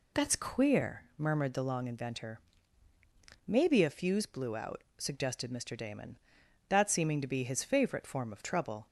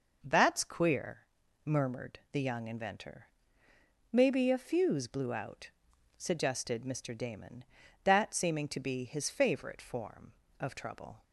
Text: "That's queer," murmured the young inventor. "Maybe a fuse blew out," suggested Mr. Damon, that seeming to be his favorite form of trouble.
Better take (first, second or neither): second